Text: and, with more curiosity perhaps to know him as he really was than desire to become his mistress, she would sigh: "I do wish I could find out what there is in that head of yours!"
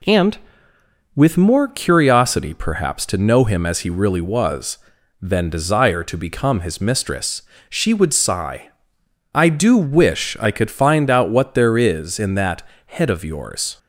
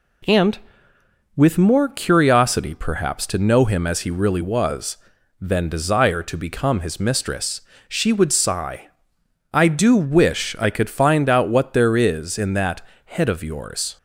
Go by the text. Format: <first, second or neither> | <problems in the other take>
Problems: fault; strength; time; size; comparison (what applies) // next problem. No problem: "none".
neither | pauses between "that" and "head"; slight; the same in both